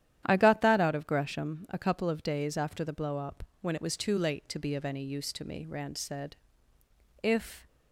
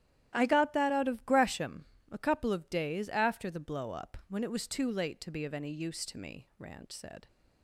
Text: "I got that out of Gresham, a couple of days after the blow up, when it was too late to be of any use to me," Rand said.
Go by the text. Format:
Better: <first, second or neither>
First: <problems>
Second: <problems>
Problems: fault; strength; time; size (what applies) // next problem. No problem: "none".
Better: second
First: starts louder than the rest; strong; until 1.2 s; 11 dB // goes on to say "If"; slight; from 7.2 s on; 0.44 s long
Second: starts louder than the rest; strong; until 1.3 s; 12 dB